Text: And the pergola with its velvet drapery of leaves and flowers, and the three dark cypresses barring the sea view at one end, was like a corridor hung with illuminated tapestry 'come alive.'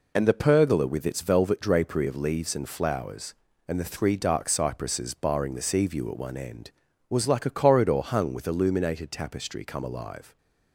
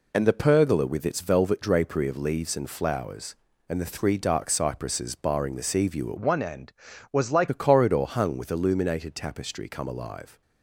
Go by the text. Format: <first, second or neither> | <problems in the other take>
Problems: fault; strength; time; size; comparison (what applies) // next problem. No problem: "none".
first | changes voice from "one" to "like"; from 6.1 to 7.4 s; 1.3 s long